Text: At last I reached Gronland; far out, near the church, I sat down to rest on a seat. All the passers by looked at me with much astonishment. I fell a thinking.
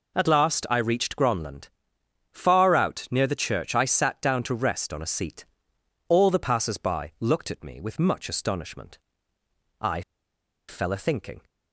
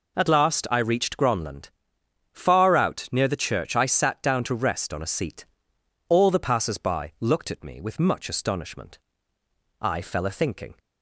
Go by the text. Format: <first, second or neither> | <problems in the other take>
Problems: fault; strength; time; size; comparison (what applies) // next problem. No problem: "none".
second | pauses between "I" and "fell"; noticeable; at 10.0 s; 0.67 s long